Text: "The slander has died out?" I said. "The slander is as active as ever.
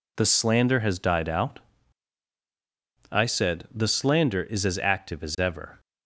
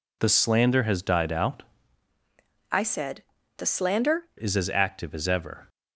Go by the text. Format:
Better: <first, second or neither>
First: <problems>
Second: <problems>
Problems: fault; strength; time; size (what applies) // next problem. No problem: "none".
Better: first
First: none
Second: changes voice from "I" to "slander"; from 2.7 to 4.2 s; 1.5 s long